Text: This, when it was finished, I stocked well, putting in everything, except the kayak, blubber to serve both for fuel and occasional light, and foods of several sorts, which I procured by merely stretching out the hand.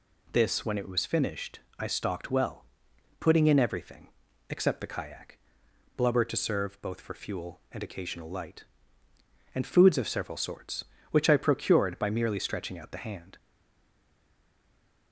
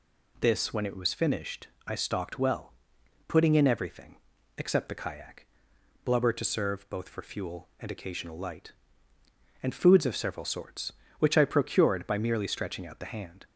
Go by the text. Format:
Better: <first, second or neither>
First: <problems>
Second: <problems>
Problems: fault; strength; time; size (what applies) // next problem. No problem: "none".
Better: second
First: stays silent after the last word; noticeable; from 13.3 s on; 1.8 s long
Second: none